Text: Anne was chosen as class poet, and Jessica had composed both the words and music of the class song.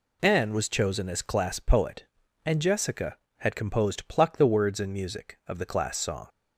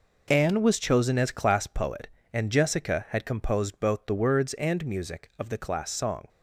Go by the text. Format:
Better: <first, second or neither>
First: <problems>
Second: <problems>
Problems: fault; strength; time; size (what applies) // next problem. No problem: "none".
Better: second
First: says "pluck" for "both"; at 4.0 s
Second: none